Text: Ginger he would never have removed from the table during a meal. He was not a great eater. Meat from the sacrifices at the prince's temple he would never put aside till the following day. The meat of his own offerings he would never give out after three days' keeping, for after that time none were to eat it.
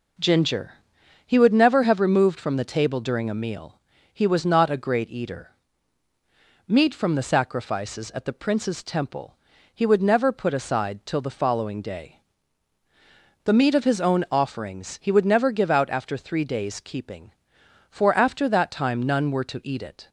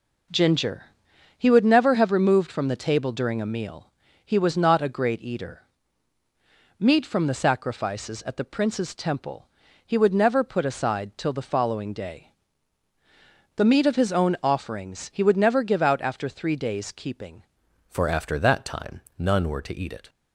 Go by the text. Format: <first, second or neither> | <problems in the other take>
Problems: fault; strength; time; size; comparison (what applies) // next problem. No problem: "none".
first | pauses between "Ginger" and "he"; noticeable; at 0.8 s; 0.52 s long; noticeable in the first // pauses between "temple" and "he"; at 9.4 s; 0.40 s long; also in the first // changes voice at "for"; from 17.9 s on; 2.1 s long // pauses between "time" and "none"; slight; at 19.0 s; 0.18 s long